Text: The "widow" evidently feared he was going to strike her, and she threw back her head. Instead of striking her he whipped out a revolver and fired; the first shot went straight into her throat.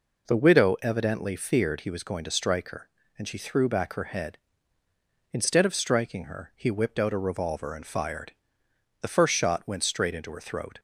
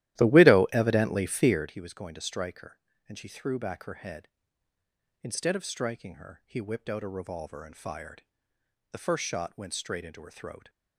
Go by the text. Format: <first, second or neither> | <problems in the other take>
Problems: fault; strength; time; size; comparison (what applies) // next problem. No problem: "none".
first | starts louder than the rest; strong; until 1.7 s; 14 dB